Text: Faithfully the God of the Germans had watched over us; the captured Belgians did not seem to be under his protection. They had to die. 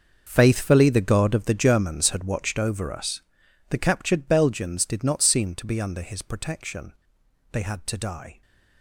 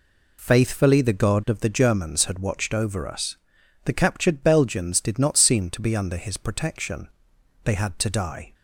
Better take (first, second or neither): second